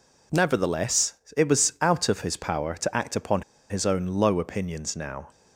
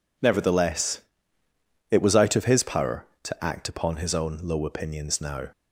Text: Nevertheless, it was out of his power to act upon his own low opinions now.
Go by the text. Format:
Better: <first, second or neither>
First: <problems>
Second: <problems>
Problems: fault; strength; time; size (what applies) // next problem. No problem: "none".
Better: second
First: pauses between "upon" and "his"; slight; at 3.4 s; 0.28 s long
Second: none